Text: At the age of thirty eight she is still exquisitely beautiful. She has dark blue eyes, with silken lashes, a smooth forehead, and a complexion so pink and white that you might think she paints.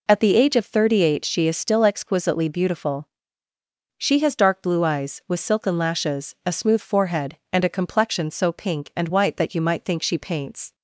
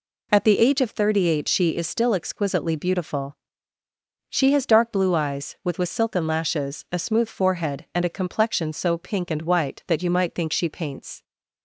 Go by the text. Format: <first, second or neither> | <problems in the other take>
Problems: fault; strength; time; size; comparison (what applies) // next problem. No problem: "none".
first | says "with" twice; at 5.7 s